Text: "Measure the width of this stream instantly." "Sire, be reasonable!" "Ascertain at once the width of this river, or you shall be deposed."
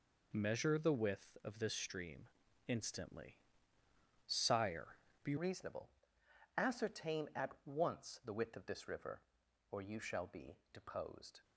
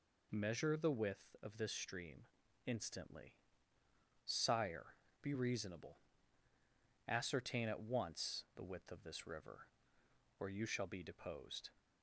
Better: second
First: pauses between "stream" and "instantly"; at 2.2 s; 0.40 s long // changes voice at "reasonable"; from 5.3 s on; 6.1 s long // pauses between "be" and "deposed"; slight; at 10.5 s; 0.16 s long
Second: pauses between "stream" and "instantly"; at 2.2 s; 0.40 s long

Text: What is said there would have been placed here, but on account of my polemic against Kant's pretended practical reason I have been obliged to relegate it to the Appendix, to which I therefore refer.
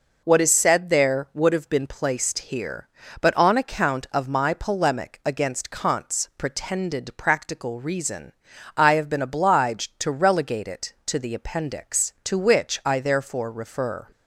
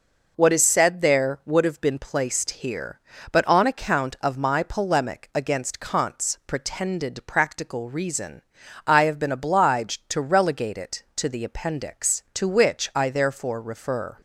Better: neither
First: pauses between "reason" and "I"; at 8.3 s; 0.43 s long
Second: pauses between "reason" and "I"; at 8.4 s; 0.44 s long

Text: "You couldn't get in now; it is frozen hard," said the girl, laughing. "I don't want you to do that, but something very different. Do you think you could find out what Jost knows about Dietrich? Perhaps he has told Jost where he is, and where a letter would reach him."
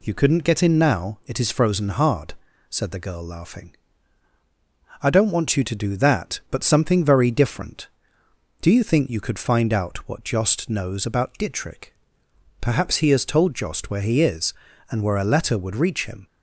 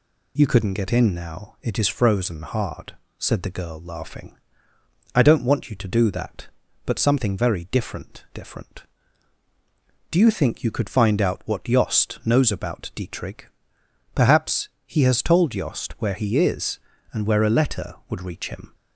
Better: first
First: none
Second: says "different" twice; at 8.3 s // pauses between "Perhaps" and "he"; slight; at 14.6 s; 0.16 s long

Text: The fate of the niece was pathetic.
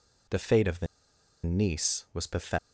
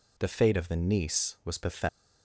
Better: second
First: pauses between "the" and "niece"; noticeable; at 0.8 s; 0.60 s long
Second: none

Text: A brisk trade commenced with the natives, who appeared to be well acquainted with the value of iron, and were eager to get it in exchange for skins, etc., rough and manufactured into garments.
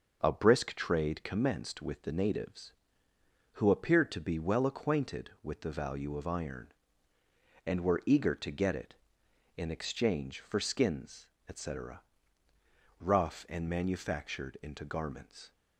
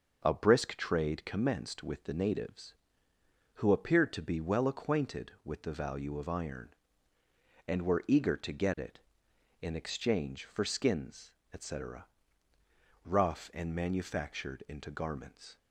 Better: neither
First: starts louder than the rest; noticeable; until 1.2 s; 6 dB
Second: starts louder than the rest; noticeable; until 1.2 s; 6 dB

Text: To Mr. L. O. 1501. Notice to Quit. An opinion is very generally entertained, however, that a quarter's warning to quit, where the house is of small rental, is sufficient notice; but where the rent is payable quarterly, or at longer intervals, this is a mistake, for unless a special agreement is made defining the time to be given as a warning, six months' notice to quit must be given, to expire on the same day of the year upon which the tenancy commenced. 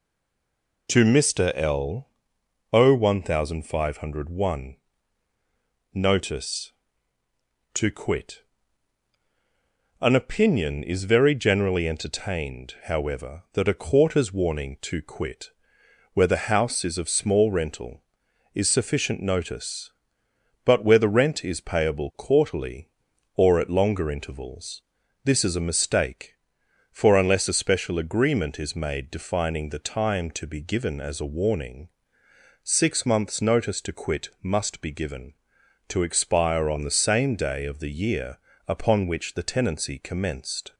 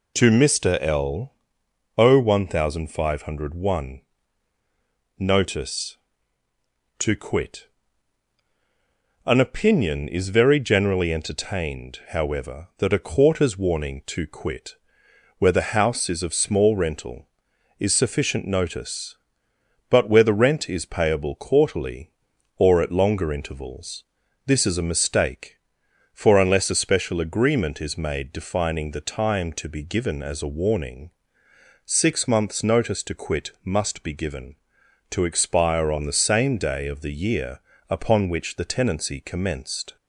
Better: second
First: stays silent before the first word; slight; until 0.8 s; 0.8 s long // pauses between "L" and "O"; noticeable; at 2.0 s; 0.64 s long // pauses between "year" and "upon"; slight; at 38.3 s; 0.30 s long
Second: pauses between "L" and "O"; noticeable; at 1.3 s; 0.64 s long // pauses between "year" and "upon"; slight; at 37.6 s; 0.30 s long

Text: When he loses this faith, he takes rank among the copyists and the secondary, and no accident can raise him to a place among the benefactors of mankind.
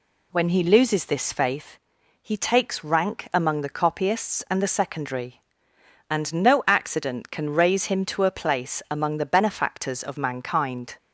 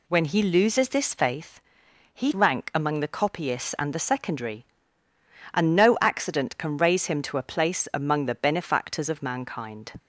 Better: first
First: none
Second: skips "takes"; at 2.3 s

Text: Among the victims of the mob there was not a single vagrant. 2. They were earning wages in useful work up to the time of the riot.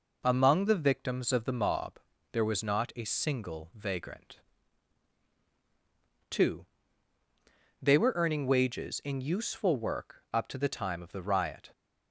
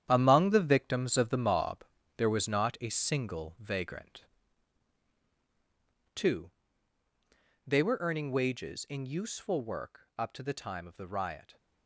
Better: first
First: pauses between "mob" and "there"; slight; at 2.0 s; 0.32 s long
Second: gets quieter; strong; throughout; 10 dB // pauses between "mob" and "there"; slight; at 1.8 s; 0.32 s long

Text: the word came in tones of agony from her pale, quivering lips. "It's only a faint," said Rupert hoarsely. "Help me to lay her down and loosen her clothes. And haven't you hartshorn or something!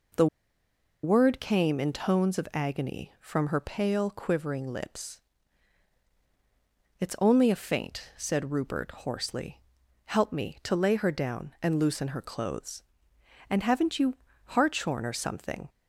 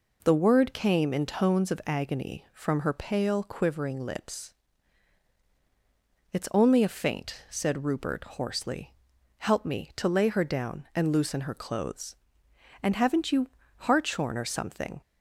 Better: second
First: pauses between "the" and "word"; noticeable; at 0.2 s; 0.77 s long // pauses between "you" and "hartshorn"; slight; at 14.1 s; 0.32 s long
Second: pauses between "you" and "hartshorn"; slight; at 13.4 s; 0.31 s long

